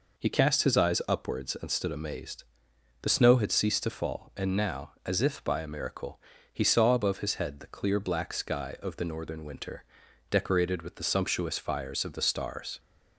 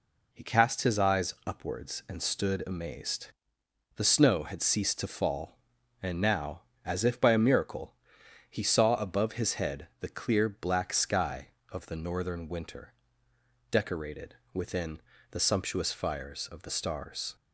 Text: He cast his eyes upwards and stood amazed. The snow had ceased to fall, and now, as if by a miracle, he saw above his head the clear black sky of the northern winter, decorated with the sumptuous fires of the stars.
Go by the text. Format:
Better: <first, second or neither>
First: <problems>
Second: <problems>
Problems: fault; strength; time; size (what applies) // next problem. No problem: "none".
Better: first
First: none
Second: says "within" for "with"; at 14.5 s